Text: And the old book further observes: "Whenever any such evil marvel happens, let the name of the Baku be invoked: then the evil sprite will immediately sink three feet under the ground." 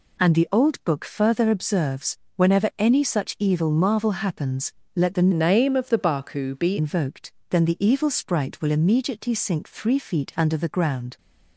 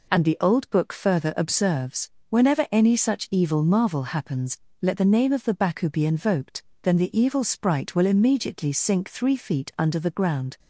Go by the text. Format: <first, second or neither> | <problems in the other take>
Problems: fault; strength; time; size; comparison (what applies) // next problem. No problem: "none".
second | changes voice from "name" to "be"; from 5.3 to 6.7 s; 1.4 s long